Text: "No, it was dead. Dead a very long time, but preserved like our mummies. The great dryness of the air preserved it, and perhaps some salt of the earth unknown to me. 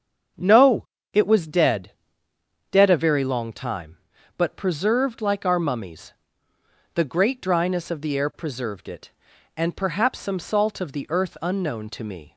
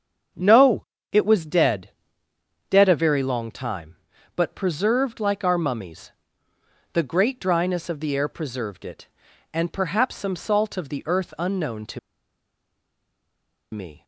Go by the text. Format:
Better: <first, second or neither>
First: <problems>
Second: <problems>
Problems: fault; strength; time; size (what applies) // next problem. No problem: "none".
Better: first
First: starts louder than the rest; until 1.6 s; 7 dB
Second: starts louder than the rest; until 1.6 s; 7 dB // pauses between "to" and "me"; strong; at 11.9 s; 1.7 s long